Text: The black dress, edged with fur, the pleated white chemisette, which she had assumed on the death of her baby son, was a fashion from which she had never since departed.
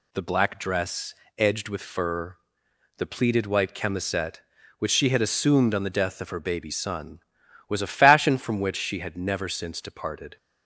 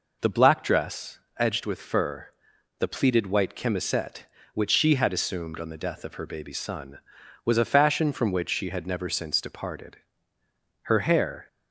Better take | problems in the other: first | goes on to say "Her hair"; noticeable; from 10.8 s on; 0.64 s long

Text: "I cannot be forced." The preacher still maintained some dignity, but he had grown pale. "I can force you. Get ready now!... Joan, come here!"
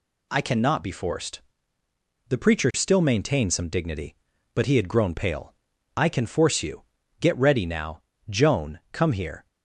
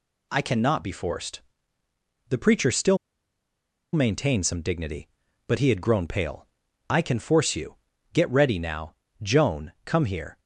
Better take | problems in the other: first | pauses between "still" and "maintained"; noticeable; at 2.9 s; 0.96 s long

